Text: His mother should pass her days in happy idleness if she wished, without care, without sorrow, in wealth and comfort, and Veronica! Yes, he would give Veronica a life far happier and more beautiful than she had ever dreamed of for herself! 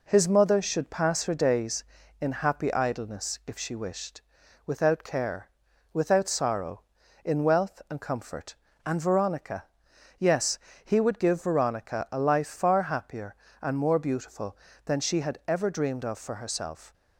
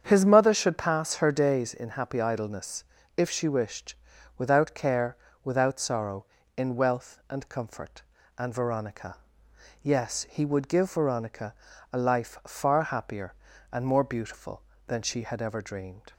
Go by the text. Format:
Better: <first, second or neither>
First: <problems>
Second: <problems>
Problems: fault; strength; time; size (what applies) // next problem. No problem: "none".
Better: first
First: none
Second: starts louder than the rest; strong; until 1.0 s; 7.5 dB // pauses between "idleness" and "if"; slight; at 2.8 s; 0.34 s long // pauses between "Veronica" and "a"; slight; at 11.5 s; 0.36 s long // stops before "of for herself"; at 16.1 s